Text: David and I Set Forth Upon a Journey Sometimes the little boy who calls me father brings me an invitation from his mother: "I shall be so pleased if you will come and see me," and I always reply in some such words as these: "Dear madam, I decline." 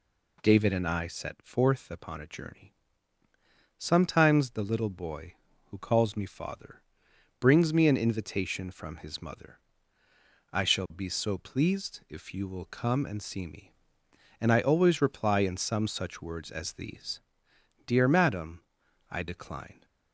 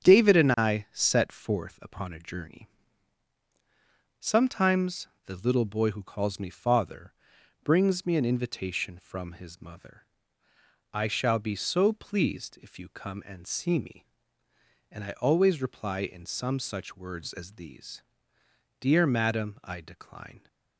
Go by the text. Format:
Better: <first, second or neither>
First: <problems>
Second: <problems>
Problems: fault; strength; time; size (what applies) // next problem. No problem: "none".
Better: first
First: pauses between "Journey" and "Sometimes"; at 2.7 s; 1.0 s long // pauses between "father" and "brings"; noticeable; at 6.8 s; 0.60 s long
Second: starts louder than the rest; strong; until 1.1 s; 8 dB // pauses between "Journey" and "Sometimes"; strong; at 2.6 s; 1.5 s long // pauses between "Sometimes" and "the"; slight; at 5.0 s; 0.18 s long // pauses between "father" and "brings"; noticeable; at 7.1 s; 0.50 s long // skips "will"; at 12.8 s